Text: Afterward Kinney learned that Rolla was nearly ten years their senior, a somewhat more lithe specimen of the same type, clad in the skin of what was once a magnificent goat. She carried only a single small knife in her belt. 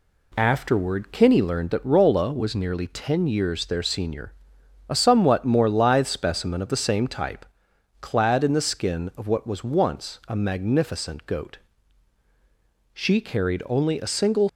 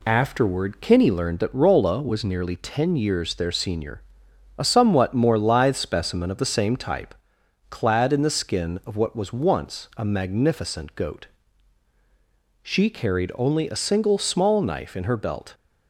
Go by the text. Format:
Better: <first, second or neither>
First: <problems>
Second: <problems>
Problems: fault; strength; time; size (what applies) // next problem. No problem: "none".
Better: second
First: stops before "small knife in her belt"; at 14.4 s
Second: none